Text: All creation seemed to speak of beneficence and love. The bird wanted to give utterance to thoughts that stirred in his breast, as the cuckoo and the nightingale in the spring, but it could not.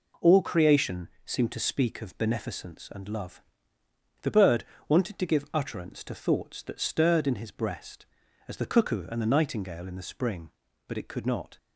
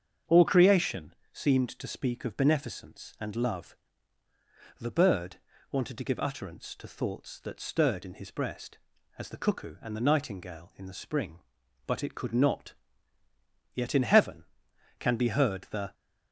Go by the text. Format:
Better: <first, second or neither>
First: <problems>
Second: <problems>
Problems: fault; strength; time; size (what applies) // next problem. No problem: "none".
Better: first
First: pauses between "creation" and "seemed"; slight; at 1.0 s; 0.16 s long // pauses between "bird" and "wanted"; slight; at 4.6 s; 0.24 s long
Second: starts louder than the rest; strong; until 1.4 s; 7 dB // pauses between "creation" and "seemed"; slight; at 1.1 s; 0.20 s long // pauses between "bird" and "wanted"; slight; at 5.3 s; 0.34 s long // goes on to say "Yet in heaven can be heard the"; strong; from 13.7 s on; 2.2 s long